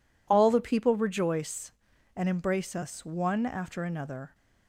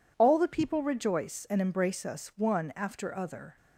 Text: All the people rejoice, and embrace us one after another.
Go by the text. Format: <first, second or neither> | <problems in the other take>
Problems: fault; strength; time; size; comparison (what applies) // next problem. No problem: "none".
first | says "other" for "another"; at 3.1 s